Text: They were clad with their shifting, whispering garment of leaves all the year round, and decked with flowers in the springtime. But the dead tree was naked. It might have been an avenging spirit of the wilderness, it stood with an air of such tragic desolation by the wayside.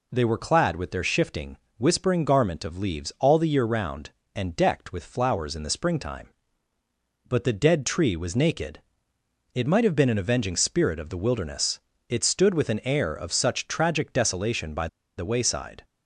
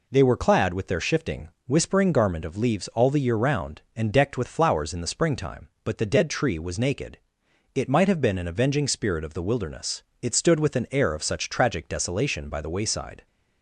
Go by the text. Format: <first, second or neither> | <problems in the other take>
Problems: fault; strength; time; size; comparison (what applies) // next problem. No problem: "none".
second | pauses between "by" and "the"; slight; at 14.8 s; 0.29 s long